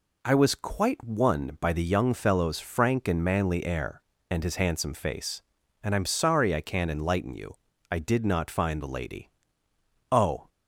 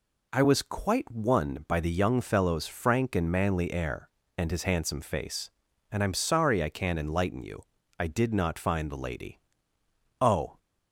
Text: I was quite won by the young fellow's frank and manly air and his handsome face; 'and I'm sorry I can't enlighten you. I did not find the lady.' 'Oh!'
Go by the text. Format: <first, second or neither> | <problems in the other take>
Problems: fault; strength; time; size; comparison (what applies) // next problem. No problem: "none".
neither | none